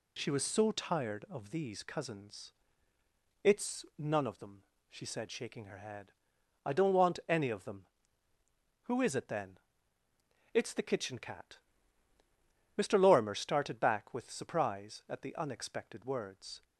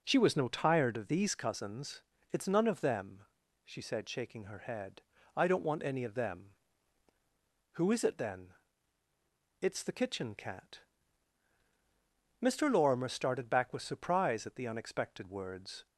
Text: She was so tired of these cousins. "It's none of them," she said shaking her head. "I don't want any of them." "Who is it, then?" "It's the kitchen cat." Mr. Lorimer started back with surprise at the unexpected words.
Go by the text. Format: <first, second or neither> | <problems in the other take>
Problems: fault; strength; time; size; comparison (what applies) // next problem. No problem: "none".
first | says "no" for "so"; at 0.3 s